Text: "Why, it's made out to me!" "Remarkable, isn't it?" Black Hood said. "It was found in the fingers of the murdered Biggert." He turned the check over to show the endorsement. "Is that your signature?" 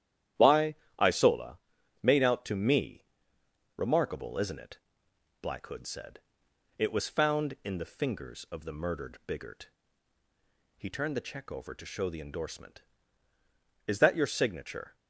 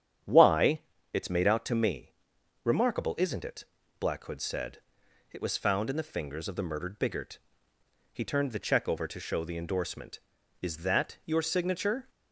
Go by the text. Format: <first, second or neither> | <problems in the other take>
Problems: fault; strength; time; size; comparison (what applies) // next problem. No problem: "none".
second | starts louder than the rest; strong; until 1.6 s; 11 dB; strong in the second // says "isola" for "it's"; at 0.9 s